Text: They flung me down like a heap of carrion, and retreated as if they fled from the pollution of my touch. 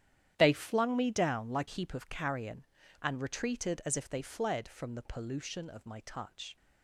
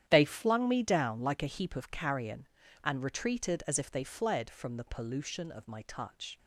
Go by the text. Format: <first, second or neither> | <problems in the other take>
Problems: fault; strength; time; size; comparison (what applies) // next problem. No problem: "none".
second | starts louder than the rest; strong; until 1.3 s; 10.5 dB; strong in the second // skips "a"; at 1.6 s